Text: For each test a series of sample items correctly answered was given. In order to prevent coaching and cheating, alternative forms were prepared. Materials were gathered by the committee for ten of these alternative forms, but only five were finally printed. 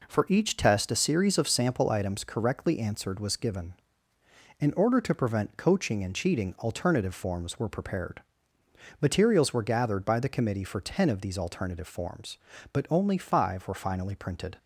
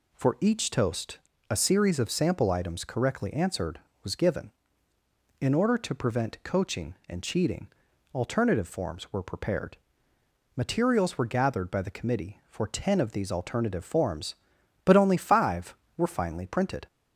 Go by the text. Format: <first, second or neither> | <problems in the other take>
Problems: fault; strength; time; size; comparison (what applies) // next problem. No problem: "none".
first | says "toast" for "test"; at 0.7 s